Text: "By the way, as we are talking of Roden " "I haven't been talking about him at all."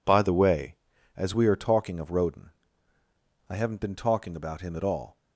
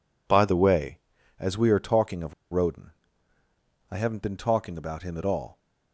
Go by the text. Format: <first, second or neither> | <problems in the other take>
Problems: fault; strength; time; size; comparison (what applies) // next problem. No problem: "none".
first | pauses between "of" and "Roden"; slight; at 2.3 s; 0.18 s long